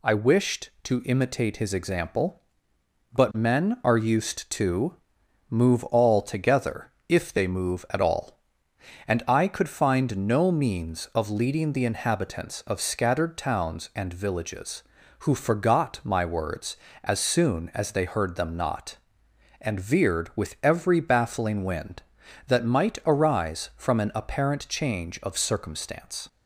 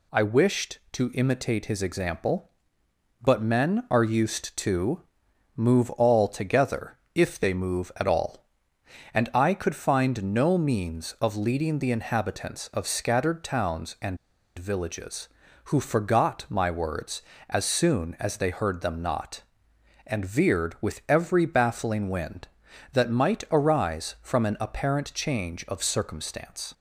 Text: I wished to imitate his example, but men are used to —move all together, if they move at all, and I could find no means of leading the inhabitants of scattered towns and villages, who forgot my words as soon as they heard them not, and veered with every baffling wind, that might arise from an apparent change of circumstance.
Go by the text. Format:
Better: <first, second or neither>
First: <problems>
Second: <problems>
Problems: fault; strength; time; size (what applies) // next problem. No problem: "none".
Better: first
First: none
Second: pauses between "and" and "villages"; at 14.1 s; 0.40 s long